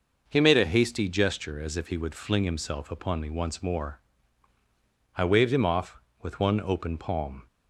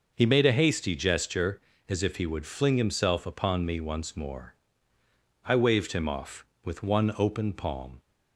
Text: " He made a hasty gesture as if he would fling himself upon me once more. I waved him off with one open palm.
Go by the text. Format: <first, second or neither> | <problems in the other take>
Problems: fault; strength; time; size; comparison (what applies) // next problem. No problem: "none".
neither | none